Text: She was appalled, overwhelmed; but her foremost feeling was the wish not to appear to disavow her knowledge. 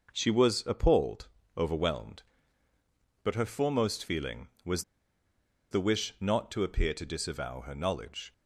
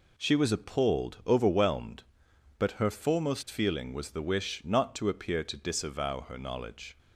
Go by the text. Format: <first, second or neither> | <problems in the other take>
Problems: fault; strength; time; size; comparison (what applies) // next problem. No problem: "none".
second | pauses between "was" and "the"; noticeable; at 4.8 s; 0.89 s long